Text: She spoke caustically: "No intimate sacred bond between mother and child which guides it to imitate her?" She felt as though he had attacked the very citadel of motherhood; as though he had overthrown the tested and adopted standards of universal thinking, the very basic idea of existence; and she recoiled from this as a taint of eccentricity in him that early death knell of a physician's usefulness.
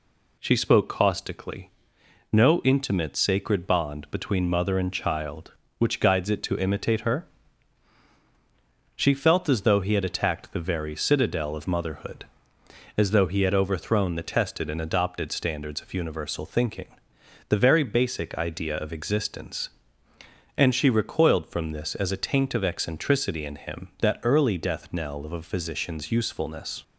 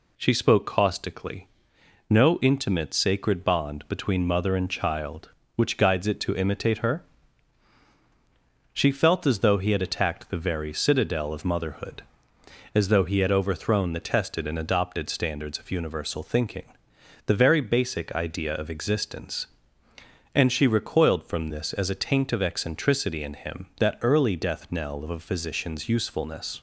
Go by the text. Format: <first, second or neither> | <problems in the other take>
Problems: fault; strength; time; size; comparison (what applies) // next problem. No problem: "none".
neither | none